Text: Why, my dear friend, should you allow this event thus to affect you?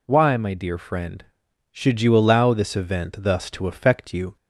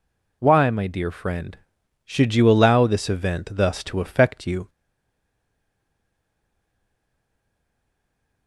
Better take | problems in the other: first | stays silent after the last word; strong; from 4.6 s on; 3.8 s long

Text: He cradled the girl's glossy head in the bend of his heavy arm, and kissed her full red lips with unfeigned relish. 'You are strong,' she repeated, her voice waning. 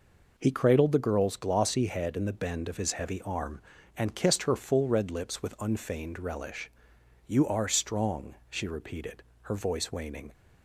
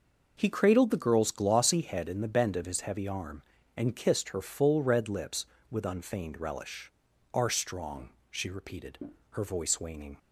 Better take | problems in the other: first | skips "You"; at 7.1 s

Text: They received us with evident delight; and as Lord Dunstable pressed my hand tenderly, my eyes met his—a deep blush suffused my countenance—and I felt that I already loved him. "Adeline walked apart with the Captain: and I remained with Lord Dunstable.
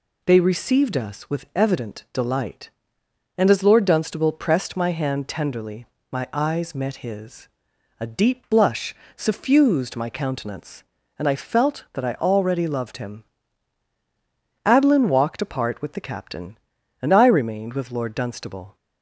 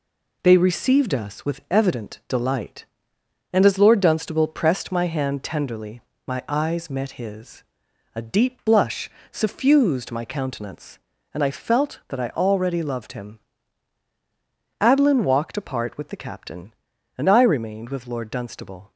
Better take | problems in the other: first | gets quieter; noticeable; throughout; 4.5 dB // pauses between "blush" and "suffused"; slight; at 9.0 s; 0.22 s long; slight in the first

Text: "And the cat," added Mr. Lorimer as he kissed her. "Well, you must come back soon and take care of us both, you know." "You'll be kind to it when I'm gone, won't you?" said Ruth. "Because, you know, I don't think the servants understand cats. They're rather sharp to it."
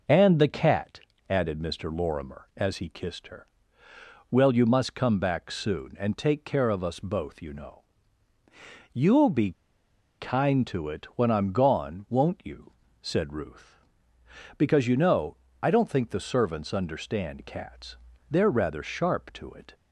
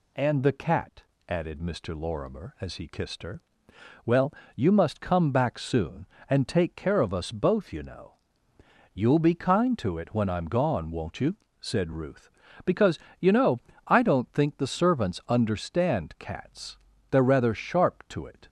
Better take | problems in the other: second | pauses between "be" and "kind"; noticeable; at 9.5 s; 0.67 s long

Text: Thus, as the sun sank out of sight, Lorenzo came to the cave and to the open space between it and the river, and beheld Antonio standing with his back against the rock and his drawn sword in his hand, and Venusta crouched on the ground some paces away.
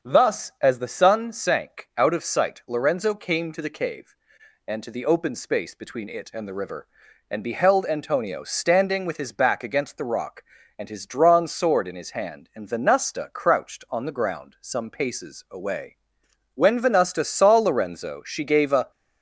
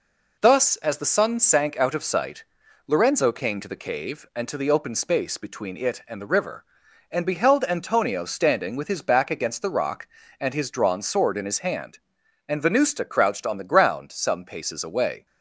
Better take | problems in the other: second | starts louder than the rest; until 1.1 s; 7 dB // goes on to say "When Venusta saw Lorenzo she gave a"; strong; from 16.5 s on; 2.3 s long

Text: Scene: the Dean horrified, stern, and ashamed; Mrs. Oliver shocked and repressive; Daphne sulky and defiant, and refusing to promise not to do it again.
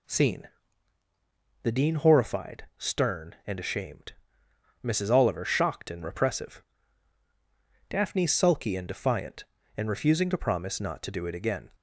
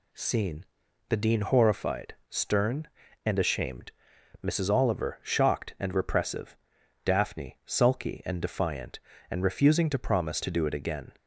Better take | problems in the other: first | skips "not"; at 10.4 s

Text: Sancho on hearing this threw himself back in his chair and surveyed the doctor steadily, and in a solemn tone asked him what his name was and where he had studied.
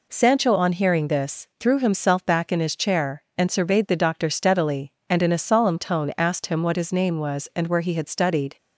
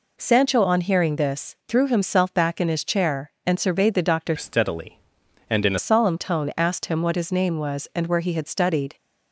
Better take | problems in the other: first | changes voice from "steadily" to "a"; from 4.3 to 5.7 s; 1.4 s long

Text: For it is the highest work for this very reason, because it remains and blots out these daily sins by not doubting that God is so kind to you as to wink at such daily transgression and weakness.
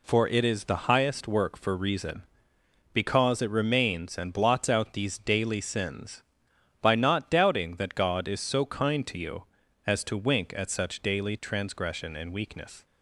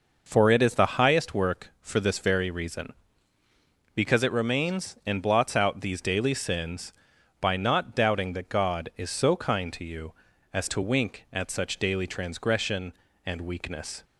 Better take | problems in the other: second | skips "this very"; at 1.7 s

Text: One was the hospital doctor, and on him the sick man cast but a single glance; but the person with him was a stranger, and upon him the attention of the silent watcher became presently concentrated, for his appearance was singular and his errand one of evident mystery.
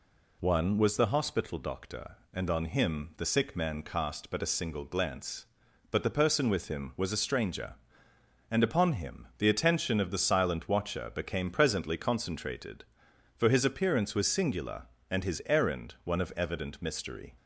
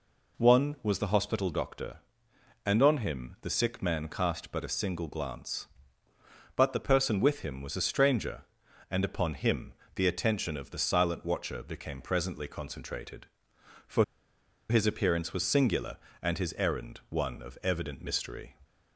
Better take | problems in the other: first | pauses between "him" and "the"; slight; at 9.7 s; 0.20 s long // pauses between "for" and "his"; noticeable; at 14.0 s; 0.65 s long

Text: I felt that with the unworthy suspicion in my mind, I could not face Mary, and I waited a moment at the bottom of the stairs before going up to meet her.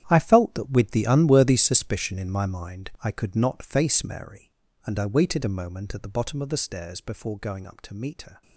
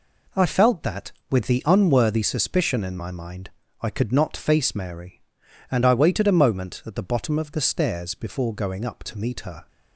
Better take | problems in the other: second | gets quieter; strong; throughout; 13.5 dB

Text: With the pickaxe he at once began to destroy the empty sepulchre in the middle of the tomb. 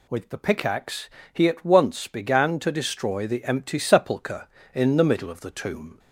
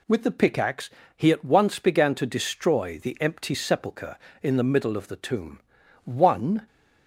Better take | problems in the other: first | pauses between "pickaxe" and "he"; slight; at 0.8 s; 0.26 s long; slight in the first // goes on to say "One"; noticeable; from 6.0 s on; 0.62 s long

